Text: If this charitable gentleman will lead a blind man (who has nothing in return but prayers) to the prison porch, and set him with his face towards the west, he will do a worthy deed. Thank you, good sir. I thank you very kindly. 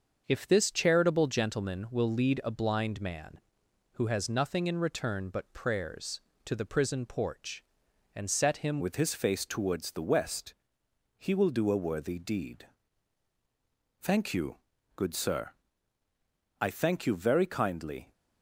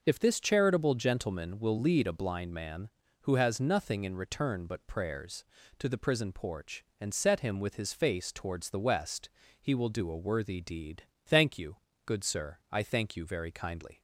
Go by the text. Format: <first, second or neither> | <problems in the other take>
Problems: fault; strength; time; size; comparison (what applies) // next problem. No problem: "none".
second | starts louder than the rest; until 1.2 s; 6.5 dB // changes voice at "with"; from 8.7 s on; 9.4 s long